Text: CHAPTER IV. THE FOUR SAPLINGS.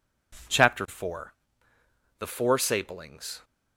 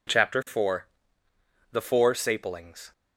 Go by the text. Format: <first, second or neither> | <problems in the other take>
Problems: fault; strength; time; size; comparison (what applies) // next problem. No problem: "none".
neither | none